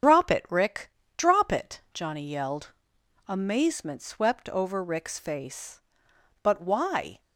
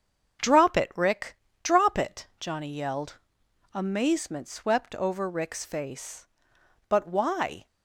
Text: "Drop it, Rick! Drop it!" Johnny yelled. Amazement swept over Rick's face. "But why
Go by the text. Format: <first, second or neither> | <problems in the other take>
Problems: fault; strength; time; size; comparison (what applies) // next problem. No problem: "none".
second | loses the start of "Drop"; at 0.0 s; 100 ms // starts louder than the rest; strong; until 1.3 s; 8 dB; strong in the second